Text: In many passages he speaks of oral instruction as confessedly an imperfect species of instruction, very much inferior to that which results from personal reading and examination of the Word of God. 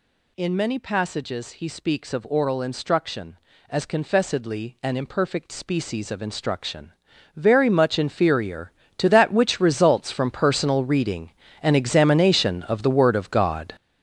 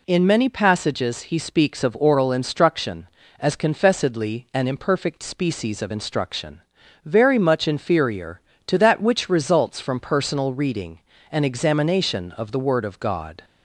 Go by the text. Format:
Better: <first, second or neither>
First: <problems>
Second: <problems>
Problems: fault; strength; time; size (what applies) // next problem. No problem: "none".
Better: second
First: gets louder; strong; throughout; 9.5 dB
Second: none